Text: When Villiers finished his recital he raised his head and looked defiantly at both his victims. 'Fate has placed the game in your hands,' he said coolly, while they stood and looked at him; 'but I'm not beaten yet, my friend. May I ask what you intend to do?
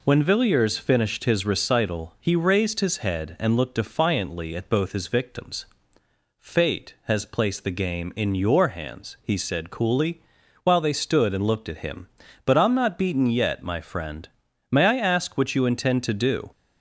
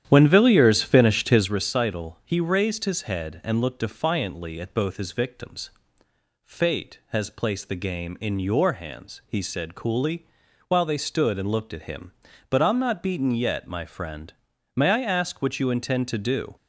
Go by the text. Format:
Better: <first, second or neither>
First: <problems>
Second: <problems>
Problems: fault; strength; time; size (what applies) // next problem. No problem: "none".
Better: first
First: none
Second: starts louder than the rest; strong; until 1.5 s; 10 dB